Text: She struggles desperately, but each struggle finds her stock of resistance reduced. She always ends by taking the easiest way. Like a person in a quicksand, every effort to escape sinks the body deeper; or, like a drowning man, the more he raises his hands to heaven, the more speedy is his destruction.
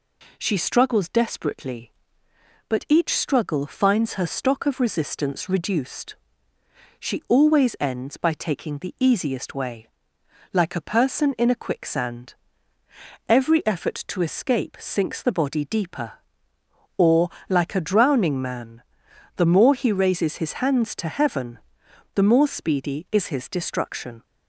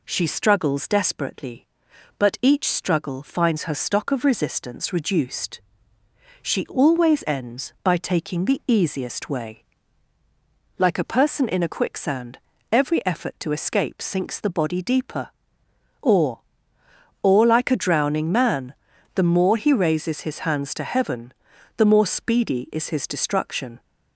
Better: first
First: none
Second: says "or" twice; at 17.2 s

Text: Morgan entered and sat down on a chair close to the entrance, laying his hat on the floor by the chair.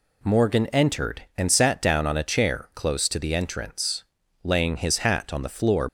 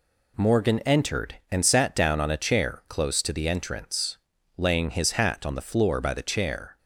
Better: second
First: stops before "by the chair"; at 5.8 s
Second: none

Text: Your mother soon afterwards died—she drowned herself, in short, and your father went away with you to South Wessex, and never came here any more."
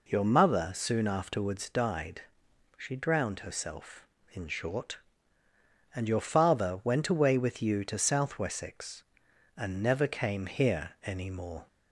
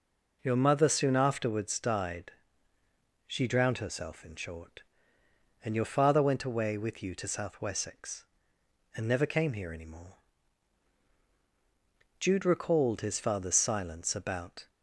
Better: first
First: none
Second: goes on to say "Jude recalled his father's silence about"; strong; from 12.2 s on; 2.4 s long

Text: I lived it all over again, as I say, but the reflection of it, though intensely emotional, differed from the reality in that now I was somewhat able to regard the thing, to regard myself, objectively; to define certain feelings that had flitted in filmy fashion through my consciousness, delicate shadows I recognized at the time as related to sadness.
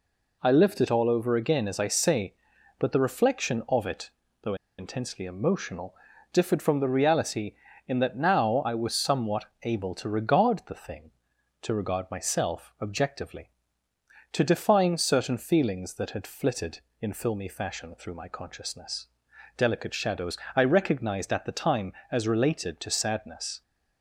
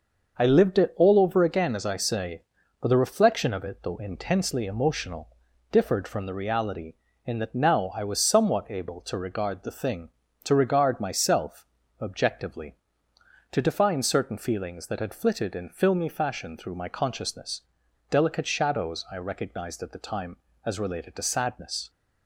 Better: second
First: pauses between "though" and "intensely"; slight; at 4.5 s; 0.24 s long // pauses between "somewhat" and "able"; slight; at 9.4 s; 0.16 s long // pauses between "shadows" and "I"; slight; at 20.3 s; 0.20 s long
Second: none

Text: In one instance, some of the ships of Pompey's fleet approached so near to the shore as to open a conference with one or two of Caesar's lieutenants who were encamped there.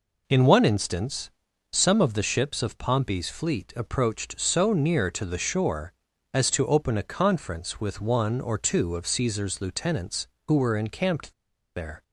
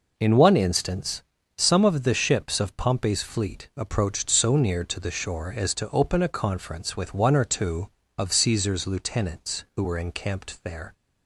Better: second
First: pauses between "encamped" and "there"; at 11.3 s; 0.42 s long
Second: none

